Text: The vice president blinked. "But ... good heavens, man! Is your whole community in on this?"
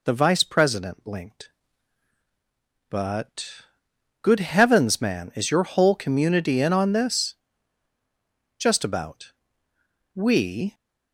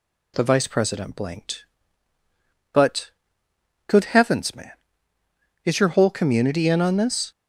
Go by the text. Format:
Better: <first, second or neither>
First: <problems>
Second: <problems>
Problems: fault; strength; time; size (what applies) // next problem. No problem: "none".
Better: second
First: goes on to say "Just about We"; strong; from 8.5 s on; 2.1 s long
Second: none